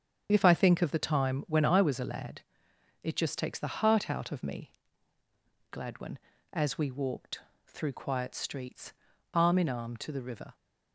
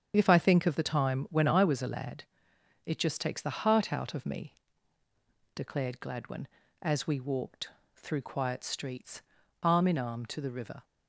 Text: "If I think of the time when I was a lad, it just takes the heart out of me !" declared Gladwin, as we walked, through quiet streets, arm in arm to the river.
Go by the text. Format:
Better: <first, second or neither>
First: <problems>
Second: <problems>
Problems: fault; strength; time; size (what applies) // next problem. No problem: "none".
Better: second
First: starts louder than the rest; strong; until 1.3 s; 8 dB // skips "declared"; at 5.7 s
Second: starts louder than the rest; strong; until 1.1 s; 8 dB